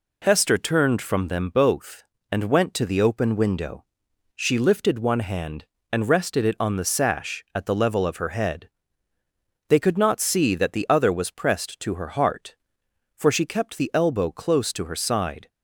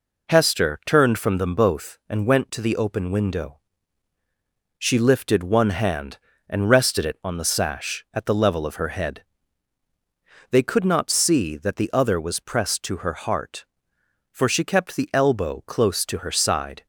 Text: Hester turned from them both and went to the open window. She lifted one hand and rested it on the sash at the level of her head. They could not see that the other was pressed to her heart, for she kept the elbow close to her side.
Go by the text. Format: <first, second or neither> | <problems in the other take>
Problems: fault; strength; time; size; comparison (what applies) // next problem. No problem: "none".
neither | none